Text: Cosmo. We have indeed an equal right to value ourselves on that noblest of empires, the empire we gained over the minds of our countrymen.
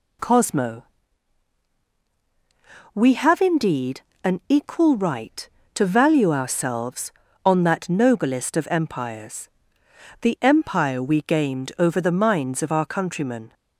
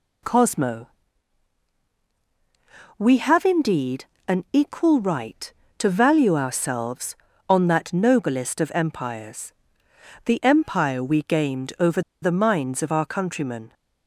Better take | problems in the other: first | pauses between "indeed" and "an"; slight; at 4.0 s; 0.20 s long; slight in the first // pauses between "over" and "the"; slight; at 12.0 s; 0.22 s long

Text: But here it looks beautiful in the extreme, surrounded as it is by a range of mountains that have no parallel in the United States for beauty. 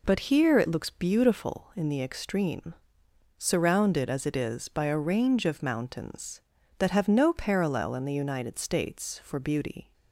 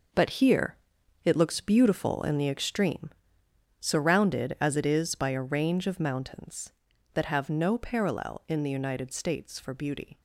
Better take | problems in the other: first | gets quieter; strong; throughout; 10 dB // pauses between "here" and "it"; noticeable; at 0.7 s; 0.46 s long

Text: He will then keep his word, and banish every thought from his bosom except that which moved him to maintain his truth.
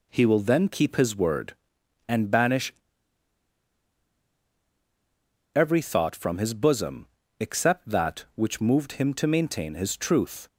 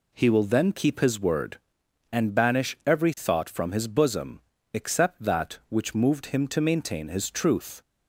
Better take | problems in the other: second | pauses between "banish" and "every"; strong; at 2.7 s; 2.8 s long // pauses between "bosom" and "except"; slight; at 7.0 s; 0.32 s long; slight in the second

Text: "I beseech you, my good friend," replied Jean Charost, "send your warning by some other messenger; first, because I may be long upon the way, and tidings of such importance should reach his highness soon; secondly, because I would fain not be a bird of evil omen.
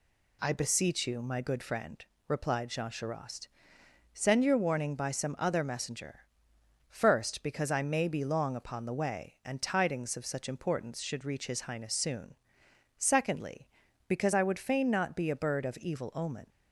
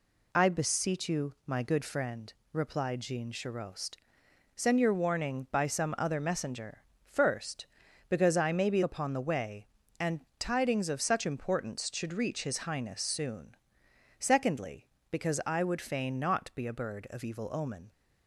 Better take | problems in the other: first | skips "long"; at 8.8 s

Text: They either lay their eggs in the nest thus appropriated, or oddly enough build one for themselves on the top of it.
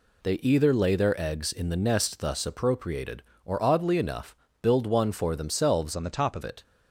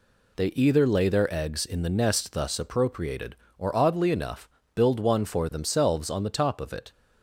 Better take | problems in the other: second | pauses between "enough" and "build"; slight; at 4.3 s; 0.26 s long; slight in the second // changes voice from "on" to "of"; from 5.9 to 6.4 s; 0.5 s long

